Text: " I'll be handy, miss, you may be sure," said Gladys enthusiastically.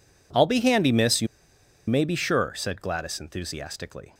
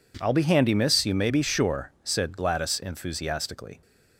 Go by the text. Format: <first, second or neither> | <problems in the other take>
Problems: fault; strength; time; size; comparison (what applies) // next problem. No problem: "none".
second | pauses between "you" and "may"; noticeable; at 1.2 s; 0.61 s long